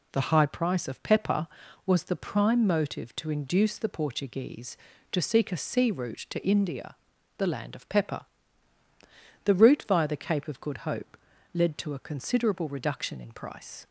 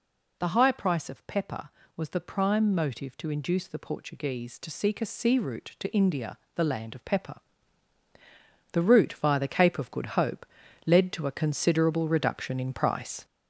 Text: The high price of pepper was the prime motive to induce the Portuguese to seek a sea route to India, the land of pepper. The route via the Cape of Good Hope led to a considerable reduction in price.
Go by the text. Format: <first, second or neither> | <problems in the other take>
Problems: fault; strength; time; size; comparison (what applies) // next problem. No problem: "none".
first | gets louder; throughout; 6 dB // pauses between "Hope" and "led"; at 10.4 s; 0.40 s long; also in the first